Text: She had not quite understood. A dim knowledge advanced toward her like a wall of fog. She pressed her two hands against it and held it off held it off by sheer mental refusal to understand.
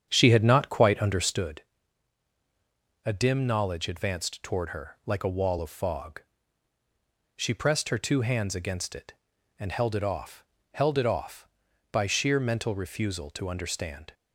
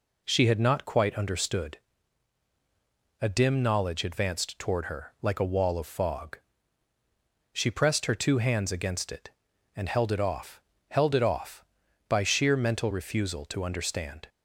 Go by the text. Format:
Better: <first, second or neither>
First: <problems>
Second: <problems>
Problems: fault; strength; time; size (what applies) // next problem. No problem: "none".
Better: second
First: starts louder than the rest; strong; until 1.5 s; 8.5 dB // pauses between "off" and "held"; slight; at 10.4 s; 0.30 s long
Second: pauses between "off" and "held"; slight; at 10.5 s; 0.30 s long